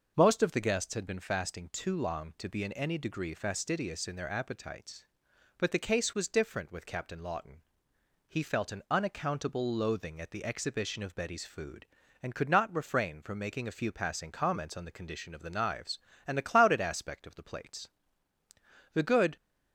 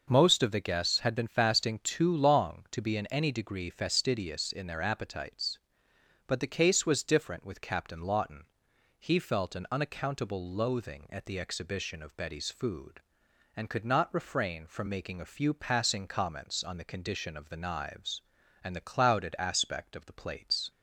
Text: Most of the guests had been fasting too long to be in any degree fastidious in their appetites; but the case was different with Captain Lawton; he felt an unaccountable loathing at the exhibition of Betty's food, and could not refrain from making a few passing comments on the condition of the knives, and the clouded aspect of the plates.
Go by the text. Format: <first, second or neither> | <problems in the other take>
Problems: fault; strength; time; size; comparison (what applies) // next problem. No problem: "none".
second | goes on to say "The good"; slight; from 18.9 s on; 0.42 s long